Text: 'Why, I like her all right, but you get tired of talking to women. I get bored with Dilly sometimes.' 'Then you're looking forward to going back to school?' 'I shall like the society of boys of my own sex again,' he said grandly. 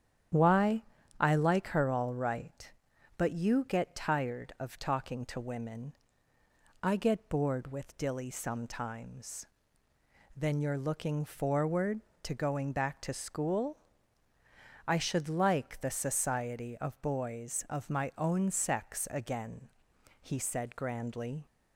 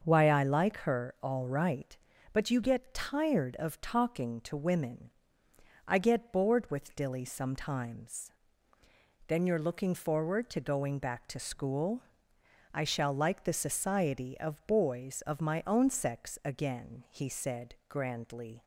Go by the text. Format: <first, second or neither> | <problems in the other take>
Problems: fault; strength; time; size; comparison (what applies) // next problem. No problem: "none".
second | starts louder than the rest; strong; until 1.7 s; 9.5 dB; also in the second // says "should" for "shall"; at 14.9 s